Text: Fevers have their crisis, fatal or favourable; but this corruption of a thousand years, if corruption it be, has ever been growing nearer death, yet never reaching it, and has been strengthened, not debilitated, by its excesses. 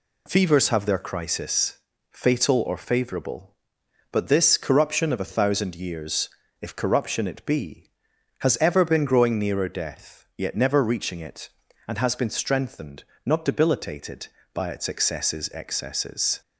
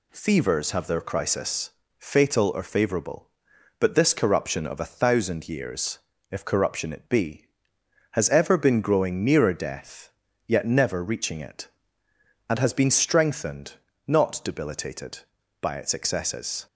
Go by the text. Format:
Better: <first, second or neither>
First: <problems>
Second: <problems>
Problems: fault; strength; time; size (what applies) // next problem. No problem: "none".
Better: second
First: says "excesses" twice; at 15.5 s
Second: none